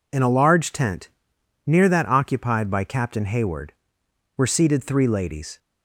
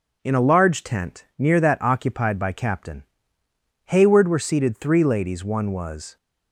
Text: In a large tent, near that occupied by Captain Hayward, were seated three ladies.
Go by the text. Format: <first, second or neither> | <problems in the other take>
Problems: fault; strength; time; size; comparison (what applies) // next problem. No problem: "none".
first | pauses between "Captain" and "Hayward"; noticeable; at 3.0 s; 0.82 s long // goes on to say "One was"; noticeable; from 5.4 s on; 0.72 s long